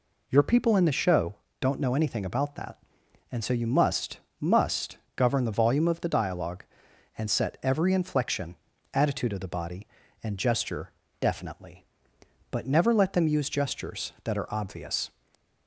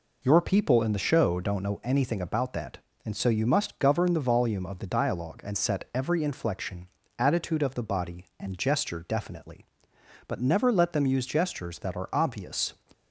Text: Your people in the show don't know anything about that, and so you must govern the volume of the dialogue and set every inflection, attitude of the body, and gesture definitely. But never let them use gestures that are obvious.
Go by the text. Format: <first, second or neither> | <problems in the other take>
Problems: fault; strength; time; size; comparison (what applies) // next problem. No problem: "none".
second | pauses between "show" and "don't"; slight; at 1.3 s; 0.24 s long // says "must" twice; at 4.4 s // pauses between "gesture" and "definitely"; slight; at 10.9 s; 0.30 s long // stays silent after the last word; slight; from 15.0 s on; 0.6 s long